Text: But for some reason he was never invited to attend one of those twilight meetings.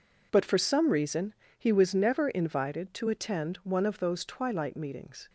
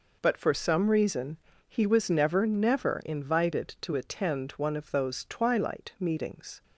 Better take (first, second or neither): first